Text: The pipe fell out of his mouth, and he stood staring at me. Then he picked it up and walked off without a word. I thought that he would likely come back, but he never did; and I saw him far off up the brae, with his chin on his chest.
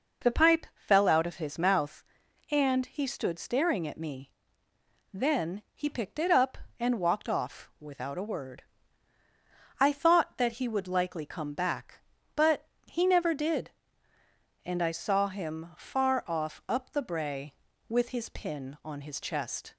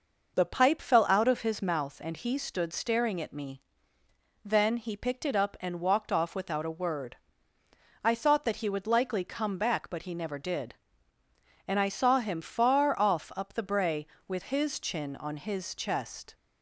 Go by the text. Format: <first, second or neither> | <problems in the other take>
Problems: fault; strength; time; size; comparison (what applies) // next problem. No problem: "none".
second | pauses between "but" and "he"; slight; at 12.6 s; 0.22 s long // says "pin" for "chin"; at 18.2 s